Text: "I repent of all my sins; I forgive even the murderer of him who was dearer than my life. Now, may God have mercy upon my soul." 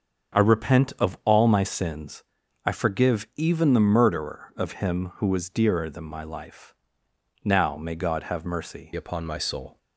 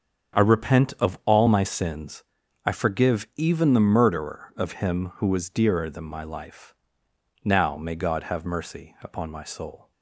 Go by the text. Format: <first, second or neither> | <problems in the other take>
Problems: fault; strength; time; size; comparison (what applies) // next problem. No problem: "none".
second | starts louder than the rest; strong; until 1.5 s; 7 dB; strong in the second // changes voice at "upon"; from 8.9 s on; 0.8 s long